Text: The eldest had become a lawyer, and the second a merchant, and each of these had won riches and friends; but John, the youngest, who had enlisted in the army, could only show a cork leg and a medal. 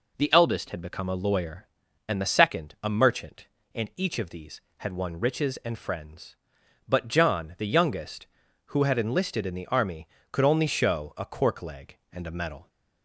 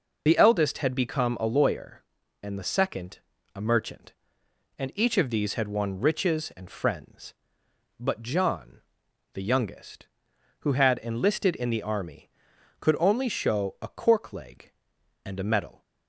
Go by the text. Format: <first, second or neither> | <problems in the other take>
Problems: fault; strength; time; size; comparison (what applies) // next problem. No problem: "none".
first | loses the start of "The"; at 0.2 s; 60 ms // pauses between "second" and "a"; slight; at 3.1 s; 0.36 s long